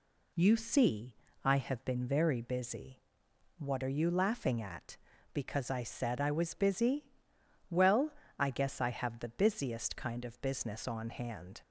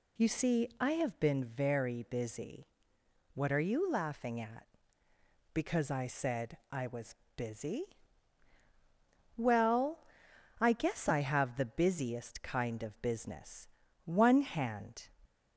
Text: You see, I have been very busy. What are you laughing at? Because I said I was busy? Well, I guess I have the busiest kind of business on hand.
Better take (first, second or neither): first